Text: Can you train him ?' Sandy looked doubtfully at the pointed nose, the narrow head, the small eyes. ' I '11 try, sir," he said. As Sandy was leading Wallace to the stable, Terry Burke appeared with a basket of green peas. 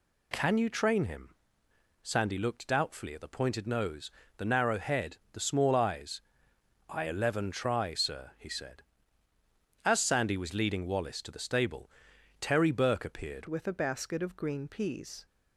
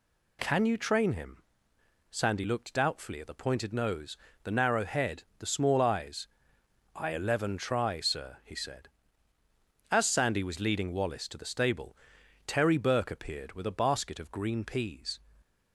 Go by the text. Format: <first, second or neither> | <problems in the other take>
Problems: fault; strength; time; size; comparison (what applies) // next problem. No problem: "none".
second | changes voice at "with"; from 13.4 s on; 1.8 s long